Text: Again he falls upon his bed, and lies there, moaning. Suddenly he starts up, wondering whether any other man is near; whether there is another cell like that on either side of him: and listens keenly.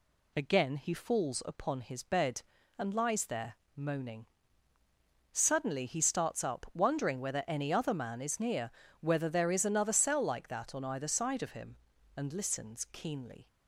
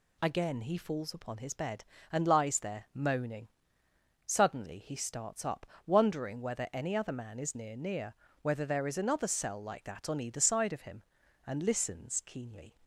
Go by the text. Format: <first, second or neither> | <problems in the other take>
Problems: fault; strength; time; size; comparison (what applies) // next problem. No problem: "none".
first | says "near" twice; at 7.7 s